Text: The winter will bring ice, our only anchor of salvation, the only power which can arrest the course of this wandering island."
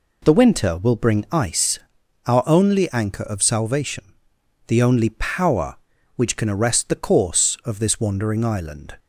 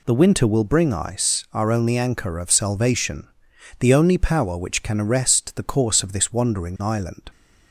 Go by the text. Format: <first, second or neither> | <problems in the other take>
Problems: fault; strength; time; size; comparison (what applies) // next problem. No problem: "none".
neither | none